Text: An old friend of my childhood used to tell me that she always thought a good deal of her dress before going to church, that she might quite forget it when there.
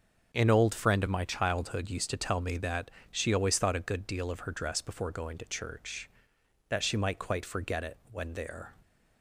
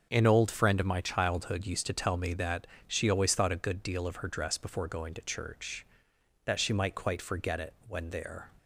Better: neither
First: starts louder than the rest; until 1.3 s; 6.5 dB // pauses between "that" and "she"; slight; at 2.9 s; 0.20 s long // pauses between "it" and "when"; slight; at 7.9 s; 0.16 s long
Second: starts louder than the rest; until 1.1 s; 6.5 dB // pauses between "that" and "she"; slight; at 2.6 s; 0.20 s long // pauses between "it" and "when"; slight; at 7.7 s; 0.16 s long

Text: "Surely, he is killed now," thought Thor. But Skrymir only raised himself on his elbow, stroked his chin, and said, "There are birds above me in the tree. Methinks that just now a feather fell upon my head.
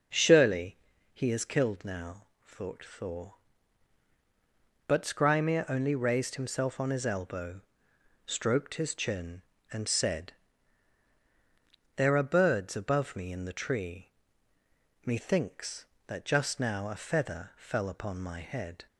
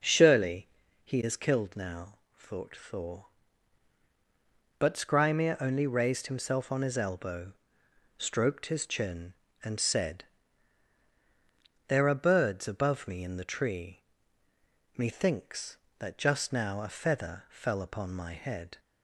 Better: neither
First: none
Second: none

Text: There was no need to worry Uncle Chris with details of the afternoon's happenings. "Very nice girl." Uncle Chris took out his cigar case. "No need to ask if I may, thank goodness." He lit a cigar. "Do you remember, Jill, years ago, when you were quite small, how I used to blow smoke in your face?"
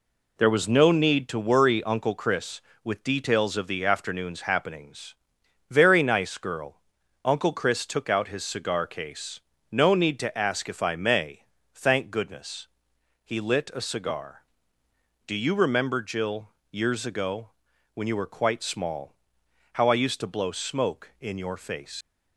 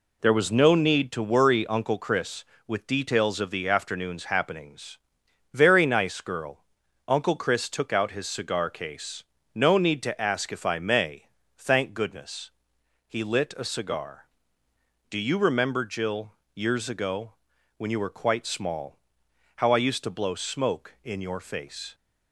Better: second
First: leaves "face" unfinished; at 22.0 s; 105 ms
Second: none

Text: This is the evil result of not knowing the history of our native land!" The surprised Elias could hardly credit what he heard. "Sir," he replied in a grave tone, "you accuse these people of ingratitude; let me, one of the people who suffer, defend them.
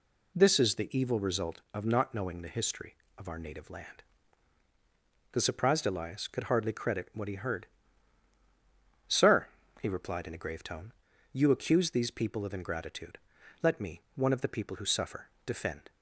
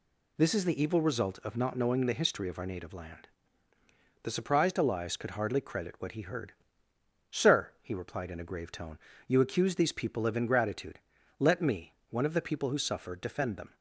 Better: second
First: stops before "them"; at 15.9 s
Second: none

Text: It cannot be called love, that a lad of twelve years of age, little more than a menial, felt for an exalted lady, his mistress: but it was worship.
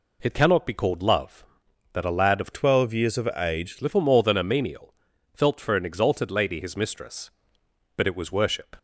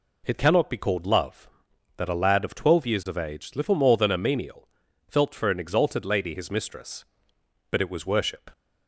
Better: second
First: changes voice from "twelve" to "age"; from 2.5 to 3.7 s; 1.2 s long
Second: none

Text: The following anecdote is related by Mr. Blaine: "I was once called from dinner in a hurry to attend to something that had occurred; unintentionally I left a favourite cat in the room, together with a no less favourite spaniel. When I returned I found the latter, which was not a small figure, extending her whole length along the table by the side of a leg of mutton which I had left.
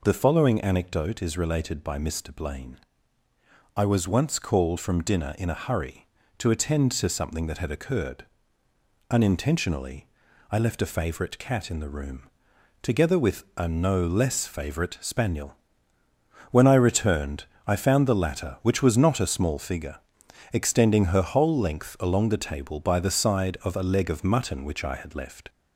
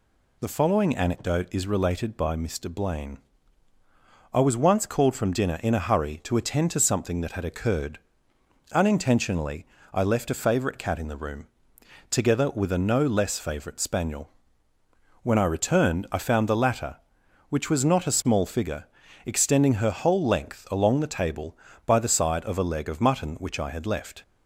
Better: second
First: gets louder; slight; throughout; 2.5 dB // pauses between "unintentionally" and "I"; noticeable; at 10.0 s; 0.46 s long // pauses between "returned" and "I"; slight; at 17.4 s; 0.24 s long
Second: pauses between "unintentionally" and "I"; slight; at 9.6 s; 0.28 s long

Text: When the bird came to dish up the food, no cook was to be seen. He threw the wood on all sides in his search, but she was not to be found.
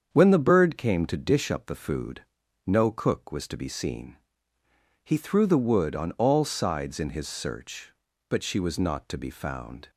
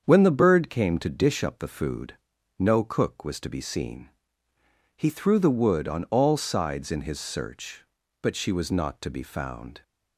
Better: neither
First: starts louder than the rest; strong; until 1.1 s; 7.5 dB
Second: starts louder than the rest; strong; until 1.0 s; 7.5 dB

